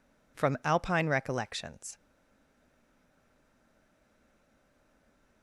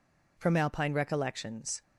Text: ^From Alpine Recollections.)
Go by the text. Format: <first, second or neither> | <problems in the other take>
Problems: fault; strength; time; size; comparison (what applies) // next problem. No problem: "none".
second | stays silent after the last word; strong; from 1.9 s on; 3.5 s long